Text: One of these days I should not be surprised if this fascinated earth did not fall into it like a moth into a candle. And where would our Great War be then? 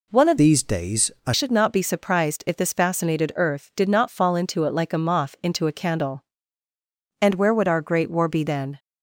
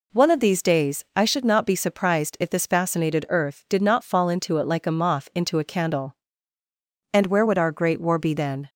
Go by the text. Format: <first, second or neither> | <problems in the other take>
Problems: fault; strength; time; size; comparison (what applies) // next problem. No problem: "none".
second | changes voice from "these" to "I"; from 0.3 to 1.3 s; 1.0 s long